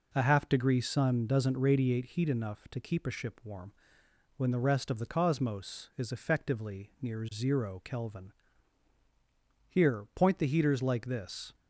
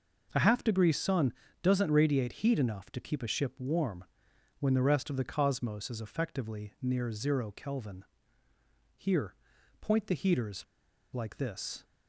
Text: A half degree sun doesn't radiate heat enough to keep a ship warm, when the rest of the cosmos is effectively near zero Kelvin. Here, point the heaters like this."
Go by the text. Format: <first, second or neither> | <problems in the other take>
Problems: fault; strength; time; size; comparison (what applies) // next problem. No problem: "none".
first | pauses between "sun" and "doesn't"; slight; at 1.3 s; 0.30 s long // pauses between "heaters" and "like"; noticeable; at 10.6 s; 0.48 s long